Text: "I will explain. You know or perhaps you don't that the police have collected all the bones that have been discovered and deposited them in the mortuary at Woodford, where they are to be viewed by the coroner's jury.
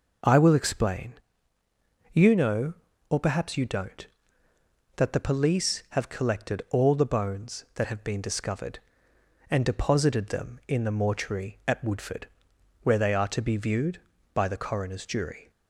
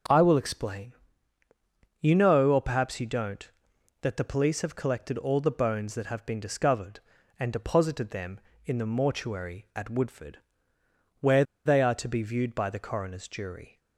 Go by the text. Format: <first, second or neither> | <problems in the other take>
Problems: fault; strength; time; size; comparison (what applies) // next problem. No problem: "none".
first | starts louder than the rest; until 2.1 s; 6 dB // pauses between "where" and "they"; slight; at 11.4 s; 0.22 s long